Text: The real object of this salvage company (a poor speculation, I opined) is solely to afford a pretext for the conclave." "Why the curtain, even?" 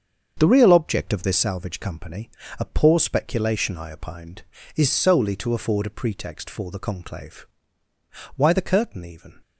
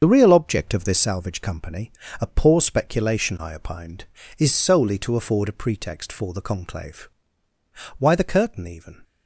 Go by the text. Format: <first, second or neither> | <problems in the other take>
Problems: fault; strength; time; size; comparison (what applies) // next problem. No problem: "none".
first | loses the start of "The"; at 0.0 s; 50 ms // starts louder than the rest; until 1.0 s; 7 dB; also in the first